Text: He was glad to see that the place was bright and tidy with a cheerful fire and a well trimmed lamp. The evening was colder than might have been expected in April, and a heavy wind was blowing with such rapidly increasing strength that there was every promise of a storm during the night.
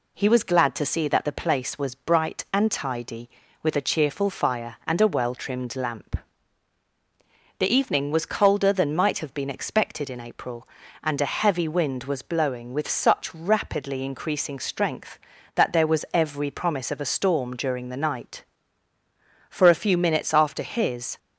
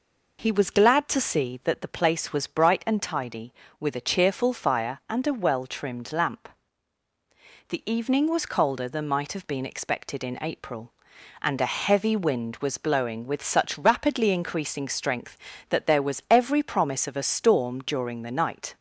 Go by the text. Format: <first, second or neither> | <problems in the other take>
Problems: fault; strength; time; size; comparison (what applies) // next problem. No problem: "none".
second | goes on to say "For a few minutes after his"; strong; from 19.4 s on; 1.6 s long